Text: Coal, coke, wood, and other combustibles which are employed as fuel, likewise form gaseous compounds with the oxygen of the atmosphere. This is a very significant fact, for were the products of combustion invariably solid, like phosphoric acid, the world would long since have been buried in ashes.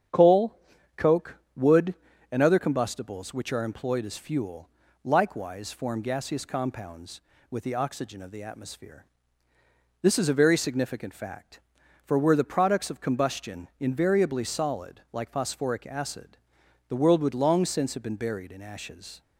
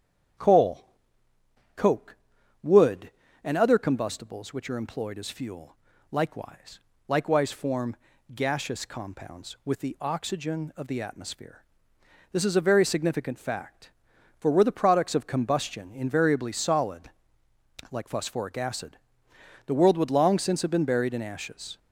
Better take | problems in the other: first | starts louder than the rest; strong; until 2.7 s; 8.5 dB; strong in the first // says "likewise" twice; at 7.0 s // pauses between "form" and "gaseous"; at 7.9 s; 0.38 s long

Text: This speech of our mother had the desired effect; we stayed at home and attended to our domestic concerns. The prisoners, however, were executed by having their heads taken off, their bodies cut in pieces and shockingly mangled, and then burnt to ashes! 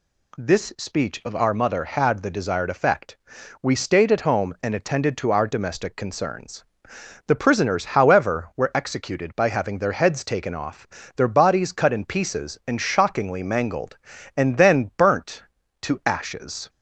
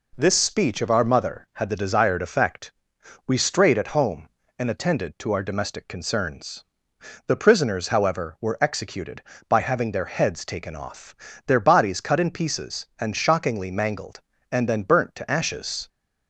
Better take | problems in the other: first | says "strayed" for "stayed"; at 3.3 s

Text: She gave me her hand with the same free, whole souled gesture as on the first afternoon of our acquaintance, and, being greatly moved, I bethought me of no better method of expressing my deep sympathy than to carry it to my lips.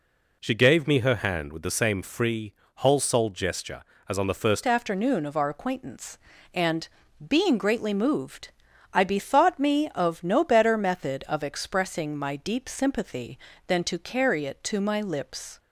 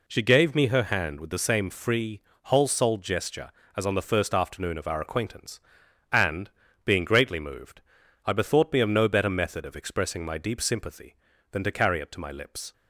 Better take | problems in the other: second | changes voice at "afternoon"; from 4.6 s on; 10.9 s long

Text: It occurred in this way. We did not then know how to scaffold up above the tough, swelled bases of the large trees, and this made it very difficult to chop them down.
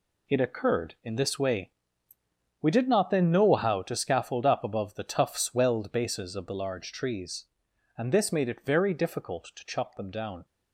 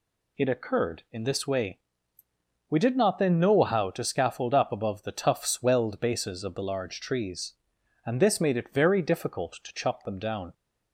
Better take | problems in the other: second | gets quieter; strong; throughout; 8.5 dB

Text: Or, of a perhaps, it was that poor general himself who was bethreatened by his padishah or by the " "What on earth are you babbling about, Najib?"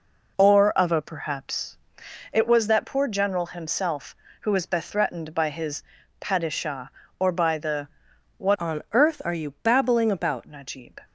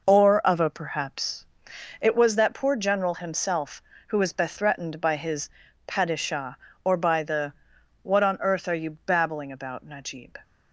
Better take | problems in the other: second | pauses between "his" and "padishah"; at 5.8 s; 0.38 s long; also in the second // changes voice from "on" to "about"; from 8.6 to 10.4 s; 1.8 s long

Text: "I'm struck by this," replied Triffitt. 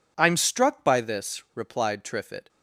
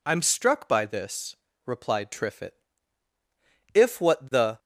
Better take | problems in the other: first | goes on to say "If what the"; noticeable; from 3.7 s on; 0.86 s long

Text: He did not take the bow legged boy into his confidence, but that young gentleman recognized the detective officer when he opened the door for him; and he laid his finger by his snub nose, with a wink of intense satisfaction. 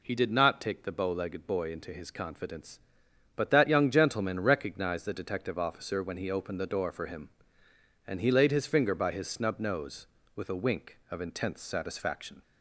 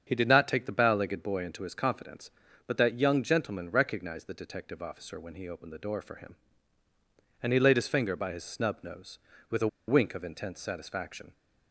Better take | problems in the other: first | starts louder than the rest; strong; until 1.0 s; 7 dB // pauses between "a" and "wink"; slight; at 9.6 s; 0.20 s long

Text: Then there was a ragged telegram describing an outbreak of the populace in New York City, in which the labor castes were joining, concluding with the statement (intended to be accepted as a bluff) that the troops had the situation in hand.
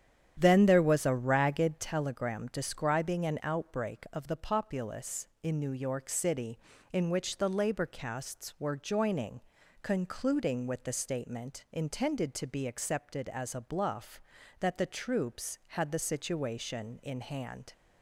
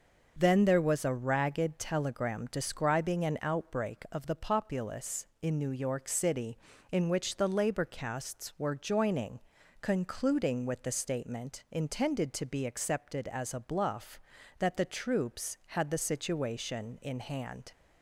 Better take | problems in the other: second | starts louder than the rest; strong; until 2.0 s; 9.5 dB

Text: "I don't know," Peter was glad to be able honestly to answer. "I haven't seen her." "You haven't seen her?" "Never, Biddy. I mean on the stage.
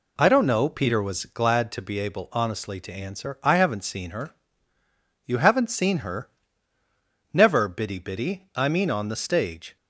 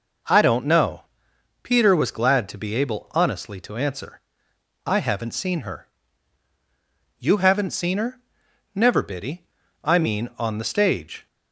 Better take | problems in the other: second | says "Biddy" twice; at 7.9 s

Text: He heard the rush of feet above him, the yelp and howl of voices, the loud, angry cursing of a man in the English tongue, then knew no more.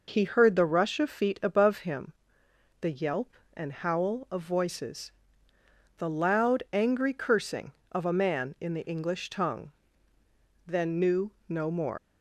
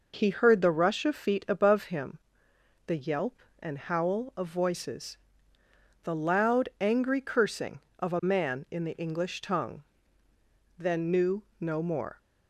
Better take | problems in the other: second | pauses between "knew" and "no"; slight; at 11.3 s; 0.16 s long; slight in the second // leaves "more" unfinished; at 11.9 s; 80 ms

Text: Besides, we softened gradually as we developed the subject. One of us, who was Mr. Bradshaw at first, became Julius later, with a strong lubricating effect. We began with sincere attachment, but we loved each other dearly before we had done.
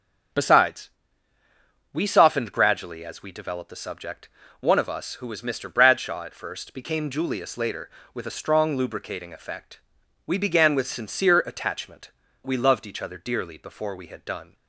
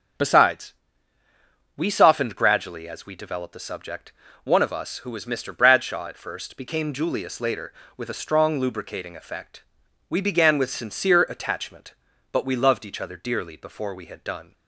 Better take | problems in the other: second | starts louder than the rest; until 2.3 s; 7 dB; also in the second // skips "but"; at 12.2 s

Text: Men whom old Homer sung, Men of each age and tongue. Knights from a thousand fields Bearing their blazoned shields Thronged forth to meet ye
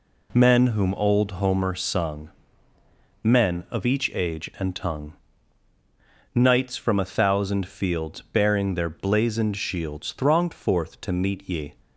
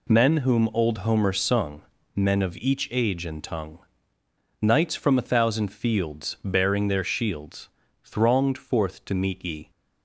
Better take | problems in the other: first | skips "blazoned"; at 7.0 s // pauses between "shields" and "Thronged"; slight; at 7.6 s; 0.36 s long

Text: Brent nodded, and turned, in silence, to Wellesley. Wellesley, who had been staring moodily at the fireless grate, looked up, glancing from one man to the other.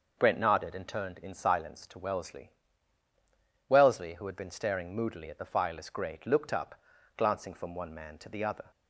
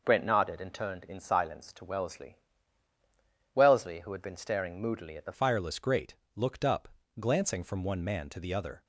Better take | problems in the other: first | changes voice at "fireless"; from 5.3 s on; 3.5 s long

